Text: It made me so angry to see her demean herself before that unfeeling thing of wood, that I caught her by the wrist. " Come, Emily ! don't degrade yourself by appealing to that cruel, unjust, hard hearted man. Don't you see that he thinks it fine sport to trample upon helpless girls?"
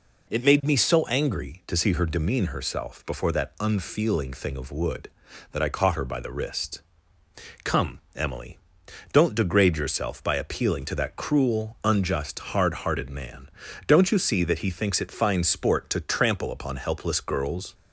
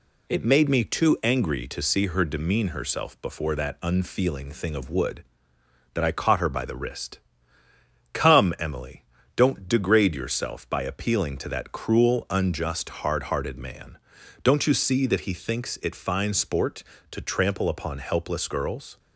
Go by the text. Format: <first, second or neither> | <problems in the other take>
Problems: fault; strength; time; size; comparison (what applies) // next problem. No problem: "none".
first | says "too" for "so"; at 0.8 s